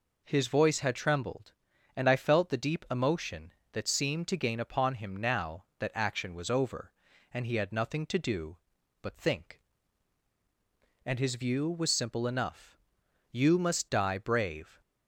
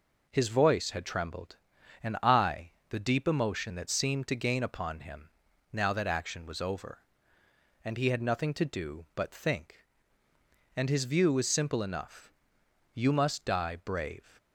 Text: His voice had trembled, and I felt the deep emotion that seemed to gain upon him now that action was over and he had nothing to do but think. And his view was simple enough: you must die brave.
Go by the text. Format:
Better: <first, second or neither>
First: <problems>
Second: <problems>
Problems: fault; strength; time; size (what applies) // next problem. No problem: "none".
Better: first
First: none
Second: skips "felt"; at 2.8 s // pauses between "him" and "now"; at 5.3 s; 0.42 s long